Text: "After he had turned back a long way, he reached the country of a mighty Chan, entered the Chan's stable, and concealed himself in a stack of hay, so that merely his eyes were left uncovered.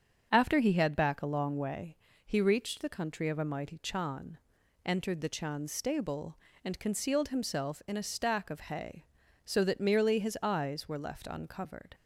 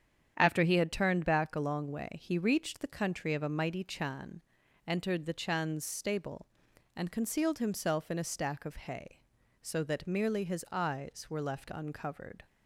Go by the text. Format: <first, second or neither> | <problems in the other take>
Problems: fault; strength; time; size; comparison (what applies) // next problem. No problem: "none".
second | starts louder than the rest; strong; until 1.3 s; 7.5 dB; strong in the second // skips "turned"; at 0.9 s